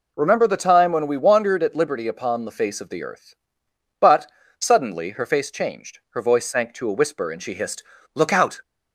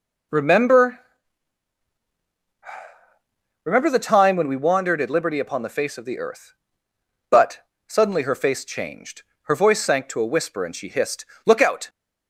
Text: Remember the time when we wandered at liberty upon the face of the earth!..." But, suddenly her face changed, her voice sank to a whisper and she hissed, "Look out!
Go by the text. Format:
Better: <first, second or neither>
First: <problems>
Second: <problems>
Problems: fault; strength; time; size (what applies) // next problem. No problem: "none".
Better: first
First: none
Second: says "Remember" twice; at 3.6 s